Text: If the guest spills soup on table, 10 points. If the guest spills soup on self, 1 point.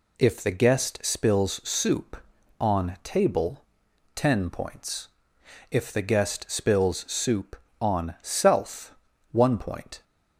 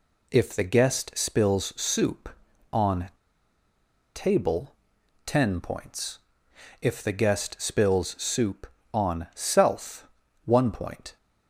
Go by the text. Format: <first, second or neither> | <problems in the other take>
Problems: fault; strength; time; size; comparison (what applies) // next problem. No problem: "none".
first | pauses between "on" and "table"; at 3.0 s; 1.0 s long